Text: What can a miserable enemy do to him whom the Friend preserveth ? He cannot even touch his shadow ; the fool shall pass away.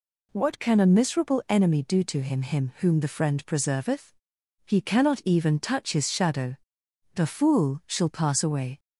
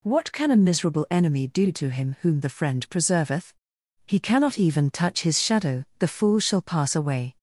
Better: second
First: says "him" twice; at 2.4 s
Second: none

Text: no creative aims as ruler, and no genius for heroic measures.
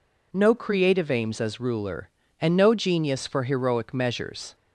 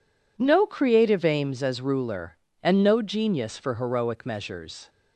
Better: neither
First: none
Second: none

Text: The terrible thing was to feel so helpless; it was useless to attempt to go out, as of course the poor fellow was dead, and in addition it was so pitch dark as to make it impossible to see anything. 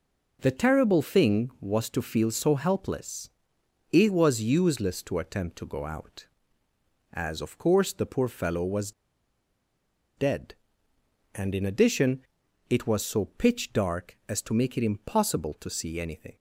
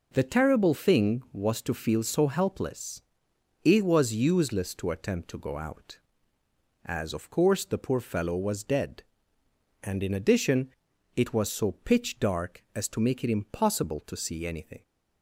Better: second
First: pauses between "was" and "dead"; strong; at 8.9 s; 1.2 s long // pauses between "addition" and "it"; noticeable; at 12.1 s; 0.50 s long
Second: pauses between "addition" and "it"; noticeable; at 10.6 s; 0.48 s long

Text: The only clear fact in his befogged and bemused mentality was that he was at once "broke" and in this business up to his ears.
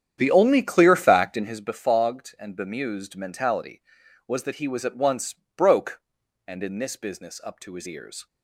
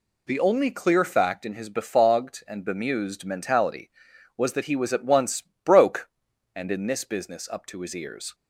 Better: second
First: starts louder than the rest; strong; until 1.7 s; 9 dB // pauses between "once" and "broke"; slight; at 5.3 s; 0.20 s long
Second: pauses between "once" and "broke"; slight; at 5.4 s; 0.20 s long

